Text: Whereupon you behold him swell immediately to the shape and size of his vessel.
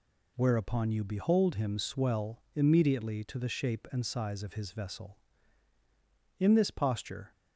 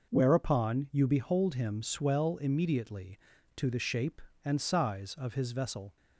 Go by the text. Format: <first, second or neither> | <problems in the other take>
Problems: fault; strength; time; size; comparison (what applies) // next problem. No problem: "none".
second | goes on to say "In this posture"; noticeable; from 6.3 s on; 0.92 s long